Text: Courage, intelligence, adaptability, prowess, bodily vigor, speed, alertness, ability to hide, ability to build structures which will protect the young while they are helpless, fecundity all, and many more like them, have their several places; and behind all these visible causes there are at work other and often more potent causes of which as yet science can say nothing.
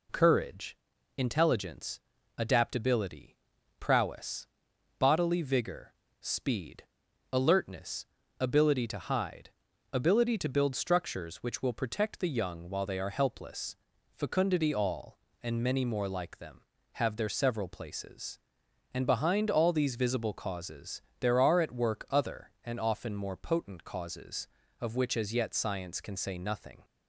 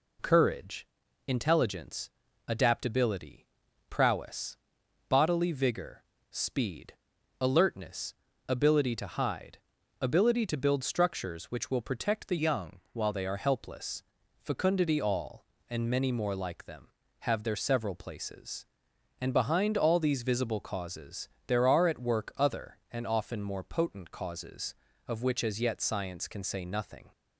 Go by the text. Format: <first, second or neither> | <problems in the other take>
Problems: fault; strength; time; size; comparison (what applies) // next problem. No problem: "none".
first | changes voice from "young" to "while"; from 12.3 to 13.1 s; 0.8 s long // pauses between "causes" and "there"; slight; at 21.2 s; 0.20 s long; slight in the first